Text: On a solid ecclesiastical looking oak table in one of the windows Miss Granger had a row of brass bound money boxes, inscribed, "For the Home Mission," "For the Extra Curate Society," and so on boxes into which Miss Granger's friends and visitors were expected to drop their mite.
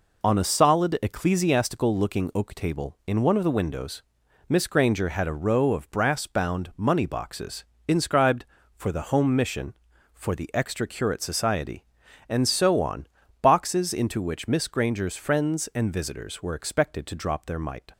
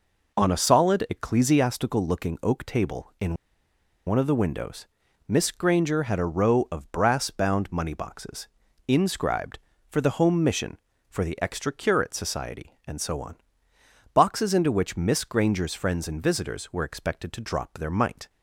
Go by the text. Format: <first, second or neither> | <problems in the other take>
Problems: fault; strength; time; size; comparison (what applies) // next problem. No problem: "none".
first | pauses between "in" and "one"; noticeable; at 3.3 s; 0.71 s long // pauses between "windows" and "Miss"; at 4.8 s; 0.40 s long; noticeable in the first // pauses between "on" and "boxes"; noticeable; at 13.3 s; 0.78 s long; slight in the first